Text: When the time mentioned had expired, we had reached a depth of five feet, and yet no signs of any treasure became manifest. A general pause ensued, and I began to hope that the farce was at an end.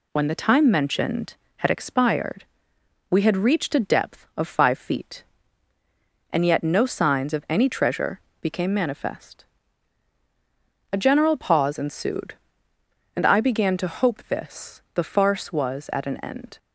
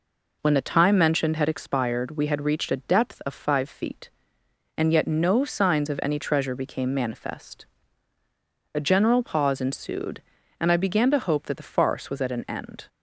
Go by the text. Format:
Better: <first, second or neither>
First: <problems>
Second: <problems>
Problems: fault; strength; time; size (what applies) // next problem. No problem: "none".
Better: second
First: pauses between "treasure" and "became"; slight; at 8.1 s; 0.22 s long // says "this" for "that"; at 14.2 s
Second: none